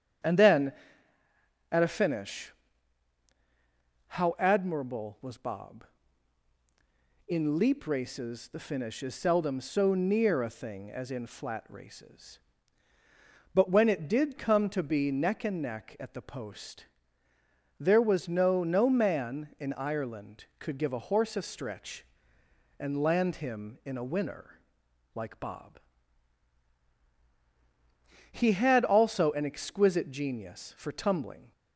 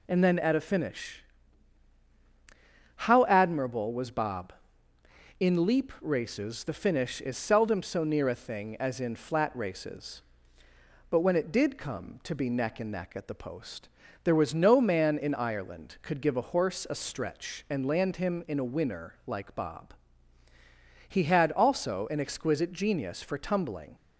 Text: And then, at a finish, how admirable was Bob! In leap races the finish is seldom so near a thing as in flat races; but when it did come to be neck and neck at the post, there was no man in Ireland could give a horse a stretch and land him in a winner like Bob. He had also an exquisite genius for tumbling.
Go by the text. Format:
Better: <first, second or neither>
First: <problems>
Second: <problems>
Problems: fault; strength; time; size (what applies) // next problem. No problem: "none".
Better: second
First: starts louder than the rest; strong; until 2.2 s; 9 dB // says "no" twice; at 18.6 s // pauses between "winner" and "like"; noticeable; at 24.5 s; 0.54 s long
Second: none